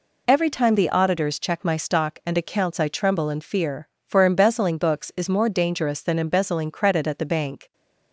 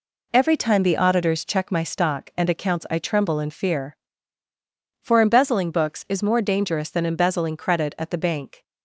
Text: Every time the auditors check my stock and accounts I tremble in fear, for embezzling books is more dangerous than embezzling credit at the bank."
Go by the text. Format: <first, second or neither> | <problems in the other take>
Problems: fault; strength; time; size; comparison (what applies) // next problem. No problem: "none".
neither | none